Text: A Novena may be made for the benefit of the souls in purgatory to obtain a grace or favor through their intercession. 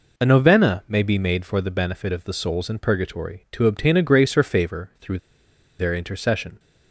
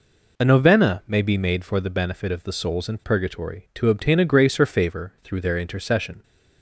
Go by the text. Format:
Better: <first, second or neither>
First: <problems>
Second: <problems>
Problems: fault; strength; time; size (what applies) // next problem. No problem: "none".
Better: second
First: pauses between "through" and "their"; noticeable; at 5.1 s; 0.61 s long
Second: none